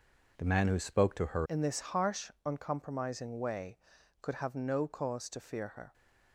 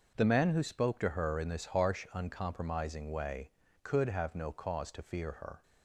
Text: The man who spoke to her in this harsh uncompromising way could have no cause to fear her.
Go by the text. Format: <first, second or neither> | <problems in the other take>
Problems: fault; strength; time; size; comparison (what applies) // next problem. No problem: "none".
second | changes voice at "in"; from 1.4 s on; 4.5 s long // pauses between "harsh" and "uncompromising"; slight; at 2.2 s; 0.16 s long